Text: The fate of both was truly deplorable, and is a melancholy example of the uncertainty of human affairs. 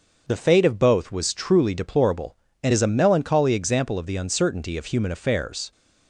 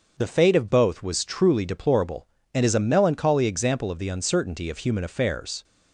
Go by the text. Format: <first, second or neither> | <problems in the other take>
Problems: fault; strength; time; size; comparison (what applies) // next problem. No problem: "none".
neither | starts louder than the rest; the same in both